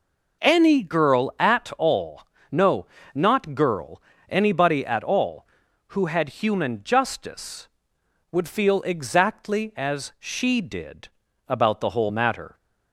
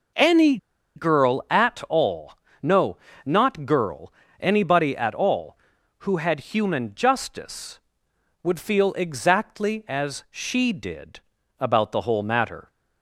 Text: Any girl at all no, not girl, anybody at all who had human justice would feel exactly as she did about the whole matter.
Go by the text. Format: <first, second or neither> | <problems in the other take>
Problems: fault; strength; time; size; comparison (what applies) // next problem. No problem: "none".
first | pauses between "Any" and "girl"; at 0.5 s; 0.38 s long // pauses between "all" and "no"; slight; at 2.3 s; 0.28 s long; slight in the first // pauses between "did" and "about"; at 11.1 s; 0.40 s long; also in the first